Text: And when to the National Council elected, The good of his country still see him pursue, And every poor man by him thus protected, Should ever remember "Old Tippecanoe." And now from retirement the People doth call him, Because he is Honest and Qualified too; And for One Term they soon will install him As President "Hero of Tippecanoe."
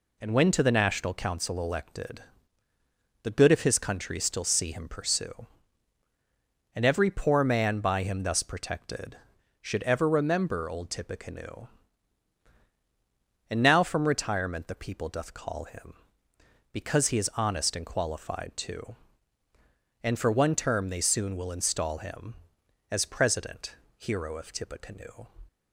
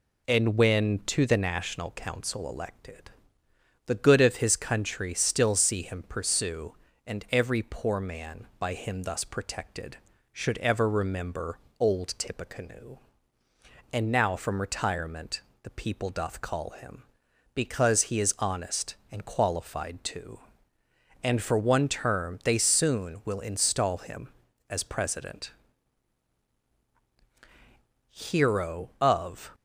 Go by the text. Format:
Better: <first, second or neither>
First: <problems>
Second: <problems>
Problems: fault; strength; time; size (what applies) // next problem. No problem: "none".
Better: first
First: pauses between "President" and "Hero"; slight; at 23.7 s; 0.22 s long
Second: pauses between "remember" and "Old"; slight; at 11.5 s; 0.20 s long // pauses between "retirement" and "the"; slight; at 15.4 s; 0.20 s long // pauses between "President" and "Hero"; strong; at 25.5 s; 2.5 s long // stops before "Tippecanoe"; at 29.5 s